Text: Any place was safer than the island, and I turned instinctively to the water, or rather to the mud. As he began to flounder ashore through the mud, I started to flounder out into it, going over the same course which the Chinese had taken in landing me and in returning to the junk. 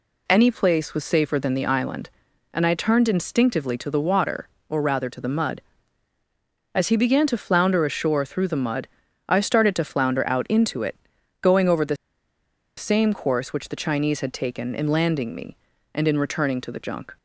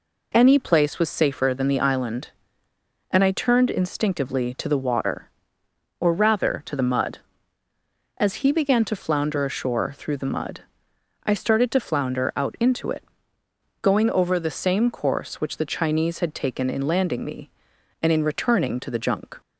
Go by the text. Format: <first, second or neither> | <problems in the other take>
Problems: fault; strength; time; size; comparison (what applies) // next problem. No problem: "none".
second | pauses between "the" and "same"; noticeable; at 11.9 s; 0.81 s long